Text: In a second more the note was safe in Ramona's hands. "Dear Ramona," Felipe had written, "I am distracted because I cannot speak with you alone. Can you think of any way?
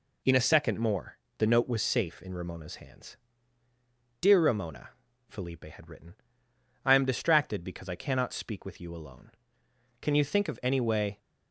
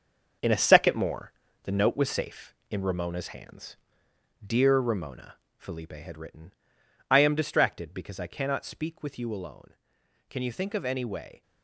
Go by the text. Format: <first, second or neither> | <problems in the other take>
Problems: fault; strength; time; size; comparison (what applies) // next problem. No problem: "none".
first | gets quieter; strong; throughout; 8 dB // pauses between "more" and "the"; slight; at 1.3 s; 0.32 s long; slight in the first